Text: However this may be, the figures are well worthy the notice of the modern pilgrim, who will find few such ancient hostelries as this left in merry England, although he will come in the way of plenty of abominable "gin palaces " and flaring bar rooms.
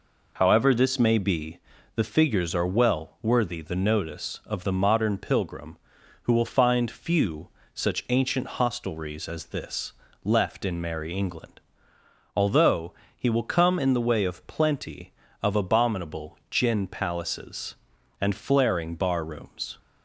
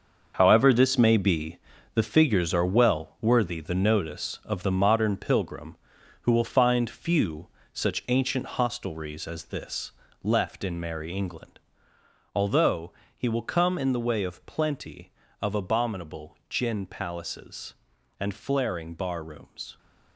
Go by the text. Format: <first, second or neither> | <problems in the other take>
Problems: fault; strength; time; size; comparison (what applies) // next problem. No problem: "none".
first | gets quieter; strong; throughout; 12 dB // pauses between "few" and "such"; slight; at 7.4 s; 0.24 s long; slight in the first // pauses between "this" and "left"; slight; at 9.9 s; 0.32 s long; slight in the first // pauses between "although" and "he"; slight; at 12.9 s; 0.24 s long; slight in the first